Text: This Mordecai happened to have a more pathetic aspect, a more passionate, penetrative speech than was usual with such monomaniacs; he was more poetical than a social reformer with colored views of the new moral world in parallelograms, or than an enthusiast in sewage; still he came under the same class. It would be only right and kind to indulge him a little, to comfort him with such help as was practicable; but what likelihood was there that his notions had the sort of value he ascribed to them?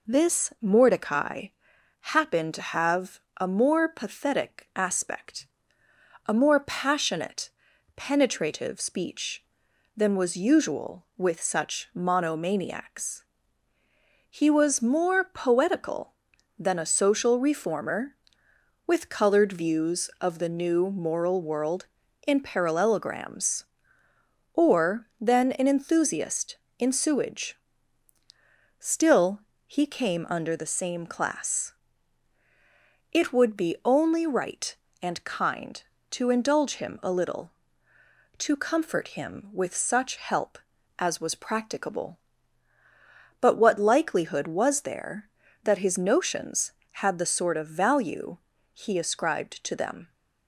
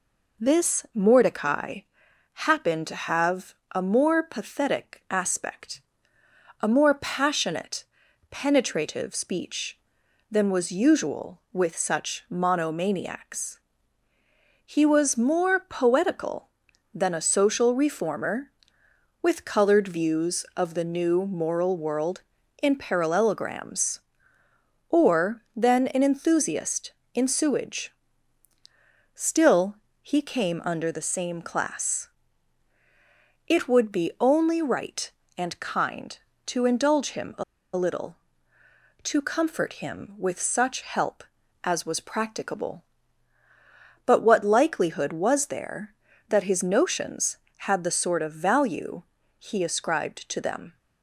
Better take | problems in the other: first | pauses between "Mordecai" and "happened"; noticeable; at 1.8 s; 0.54 s long; noticeable in the first // pauses between "have" and "a"; slight; at 3.5 s; 0.20 s long; slight in the first // pauses between "still" and "he"; slight; at 29.7 s; 0.28 s long; slight in the first // pauses between "a" and "little"; slight; at 37.4 s; 0.32 s long // pauses between "value" and "he"; at 49.0 s; 0.38 s long; also in the first

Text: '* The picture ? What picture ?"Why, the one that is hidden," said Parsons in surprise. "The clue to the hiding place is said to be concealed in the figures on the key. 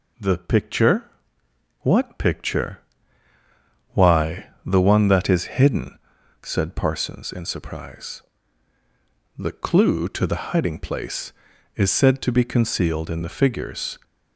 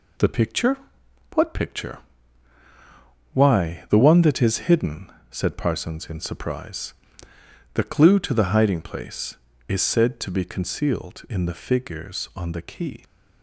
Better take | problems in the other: second | stops before "on the key"; at 14.0 s

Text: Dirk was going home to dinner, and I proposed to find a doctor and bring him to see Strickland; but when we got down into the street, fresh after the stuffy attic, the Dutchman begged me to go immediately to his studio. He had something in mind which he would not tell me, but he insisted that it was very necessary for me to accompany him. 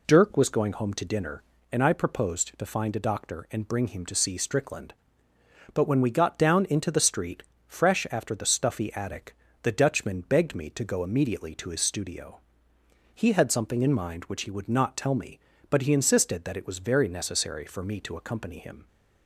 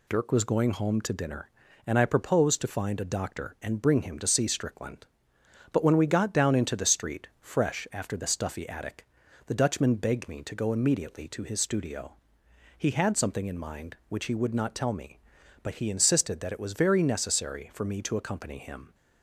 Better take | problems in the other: neither | none

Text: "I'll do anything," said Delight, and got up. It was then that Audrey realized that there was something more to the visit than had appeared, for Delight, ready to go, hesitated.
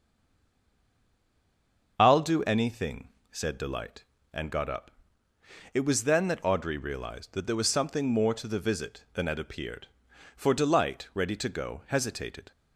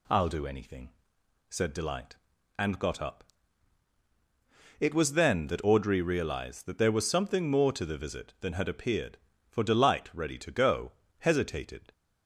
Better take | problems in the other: second | stays silent before the first word; noticeable; until 1.9 s; 1.9 s long // starts louder than the rest; until 2.9 s; 6.5 dB

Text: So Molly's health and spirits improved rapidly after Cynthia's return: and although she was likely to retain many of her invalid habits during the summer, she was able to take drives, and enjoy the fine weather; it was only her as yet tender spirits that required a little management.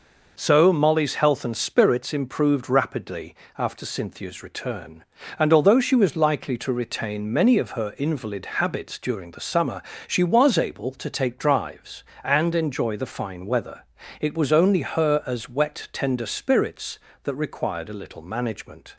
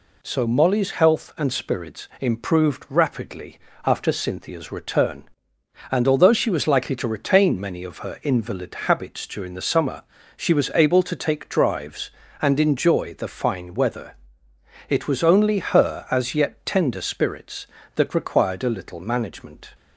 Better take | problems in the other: second | pauses between "rapidly" and "after"; slight; at 3.3 s; 0.22 s long; slight in the second // pauses between "invalid" and "habits"; slight; at 8.4 s; 0.16 s long // says "wet" for "yet"; at 15.4 s

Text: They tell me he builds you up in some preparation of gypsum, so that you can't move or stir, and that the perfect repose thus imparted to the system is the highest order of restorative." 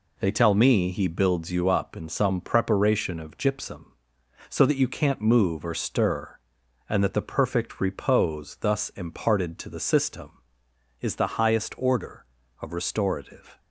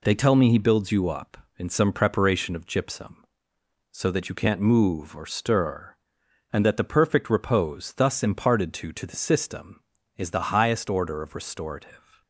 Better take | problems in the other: first | says "to" twice; at 8.9 s

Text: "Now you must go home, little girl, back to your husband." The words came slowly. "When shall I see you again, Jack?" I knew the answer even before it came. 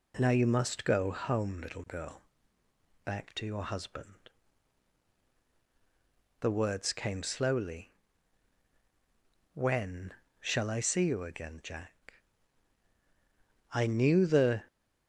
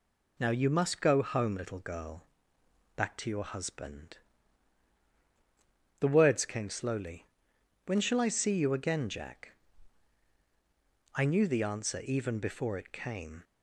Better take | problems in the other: second | pauses between "When" and "shall"; slight; at 10.1 s; 0.28 s long // stops before "answer even before it came"; at 14.6 s

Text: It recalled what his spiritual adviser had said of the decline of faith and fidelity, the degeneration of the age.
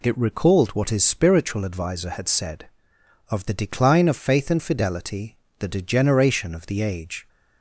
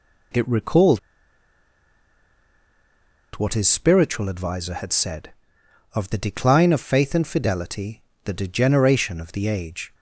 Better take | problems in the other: first | pauses between "recalled" and "what"; strong; at 0.9 s; 2.3 s long

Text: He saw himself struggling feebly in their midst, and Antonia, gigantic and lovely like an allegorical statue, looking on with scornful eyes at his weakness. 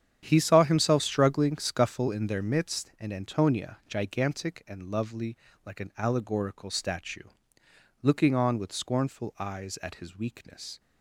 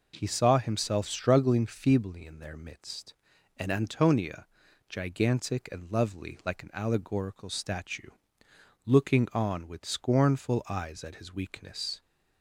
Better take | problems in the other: second | starts louder than the rest; strong; until 1.2 s; 9 dB // says "scuffle" for "feebly"; at 1.5 s // pauses between "lovely" and "like"; slight; at 5.3 s; 0.30 s long

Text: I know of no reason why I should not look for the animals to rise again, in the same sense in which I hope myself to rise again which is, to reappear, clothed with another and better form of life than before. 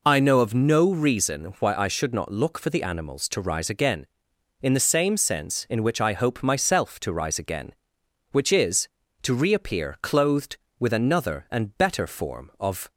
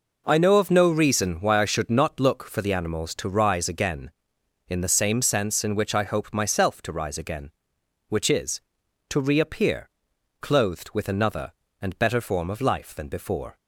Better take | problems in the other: second | stops before "life than before"; at 12.9 s

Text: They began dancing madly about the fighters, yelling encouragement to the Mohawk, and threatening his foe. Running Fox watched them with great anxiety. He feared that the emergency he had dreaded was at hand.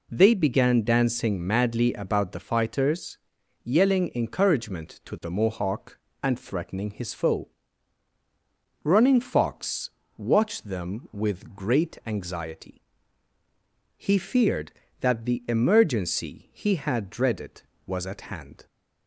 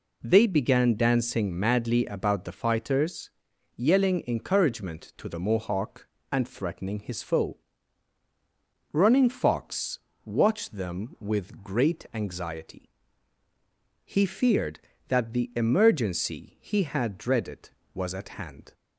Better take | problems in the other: neither | pauses between "Fox" and "watched"; slight; the same in both

